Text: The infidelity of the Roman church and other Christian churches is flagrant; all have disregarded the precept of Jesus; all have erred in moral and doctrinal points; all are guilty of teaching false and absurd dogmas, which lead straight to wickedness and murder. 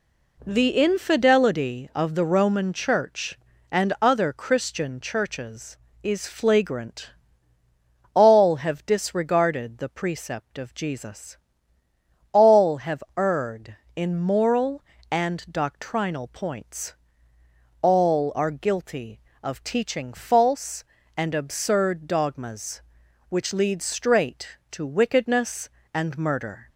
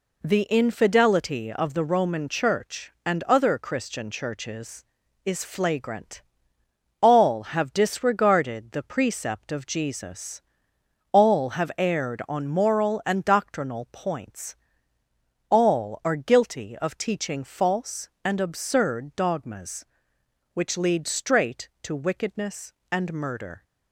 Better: first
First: none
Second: says "on" for "in"; at 12.2 s

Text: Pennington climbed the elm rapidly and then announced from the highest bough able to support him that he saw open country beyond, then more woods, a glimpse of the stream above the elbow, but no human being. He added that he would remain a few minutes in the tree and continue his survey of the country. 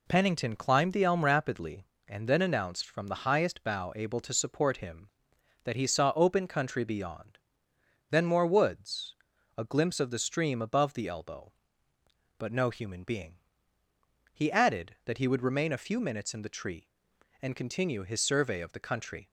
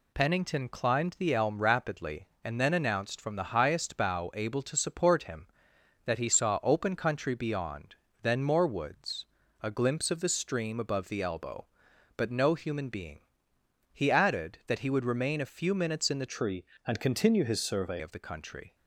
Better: first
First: none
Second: changes voice from "tree" to "survey"; from 16.2 to 17.9 s; 1.7 s long

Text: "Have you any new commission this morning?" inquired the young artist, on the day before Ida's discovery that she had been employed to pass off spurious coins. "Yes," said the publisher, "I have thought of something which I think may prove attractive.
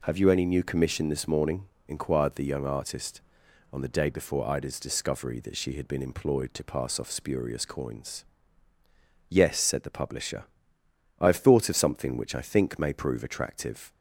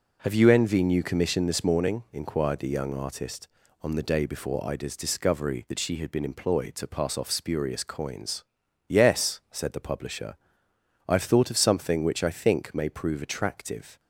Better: first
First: none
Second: says "envy" for "any"; at 0.4 s

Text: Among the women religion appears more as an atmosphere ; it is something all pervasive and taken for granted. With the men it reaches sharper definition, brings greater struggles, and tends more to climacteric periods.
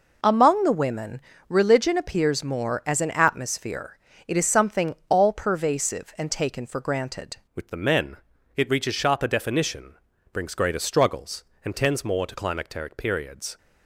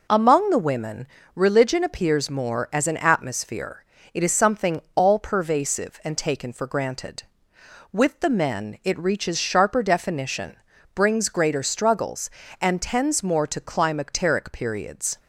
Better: second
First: pauses between "women" and "religion"; slight; at 1.2 s; 0.26 s long // changes voice at "With"; from 7.5 s on; 6.0 s long // pauses between "men" and "it"; at 8.1 s; 0.40 s long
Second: pauses between "women" and "religion"; slight; at 1.0 s; 0.26 s long

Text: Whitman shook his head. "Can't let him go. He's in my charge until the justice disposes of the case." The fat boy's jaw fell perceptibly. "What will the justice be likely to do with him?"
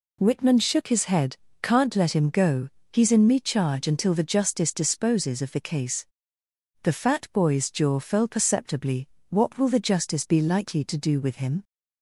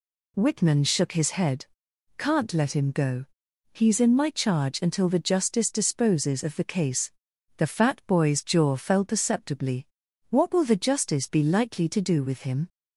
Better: second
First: says "me" for "my"; at 3.2 s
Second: none

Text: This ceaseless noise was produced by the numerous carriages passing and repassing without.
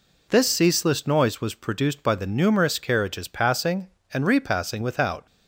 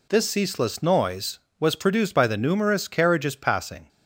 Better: first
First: none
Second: stops before "and repassing without"; at 3.8 s

